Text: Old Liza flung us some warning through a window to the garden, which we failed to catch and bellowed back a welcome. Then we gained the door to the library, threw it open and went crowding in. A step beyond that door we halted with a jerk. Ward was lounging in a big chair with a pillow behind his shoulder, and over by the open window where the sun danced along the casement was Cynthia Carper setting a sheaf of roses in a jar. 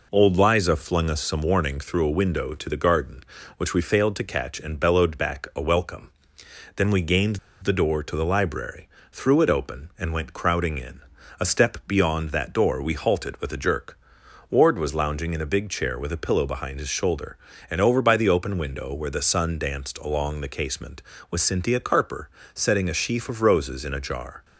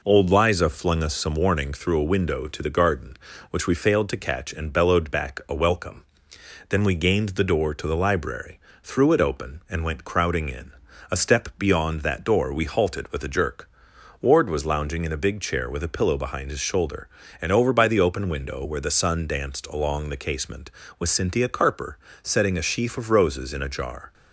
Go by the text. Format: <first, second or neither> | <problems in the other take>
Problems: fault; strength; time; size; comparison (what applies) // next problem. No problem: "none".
second | pauses between "gained" and "the"; slight; at 7.3 s; 0.24 s long // pauses between "Carper" and "setting"; slight; at 22.2 s; 0.26 s long; slight in the second